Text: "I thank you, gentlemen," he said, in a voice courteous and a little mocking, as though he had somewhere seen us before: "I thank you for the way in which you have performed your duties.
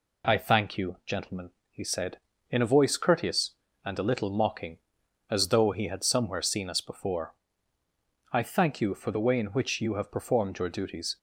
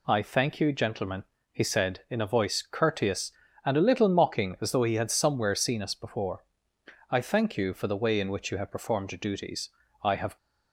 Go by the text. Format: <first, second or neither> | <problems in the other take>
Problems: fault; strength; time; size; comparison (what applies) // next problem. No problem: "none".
first | goes on to say "I have"; slight; from 10.0 s on; 0.34 s long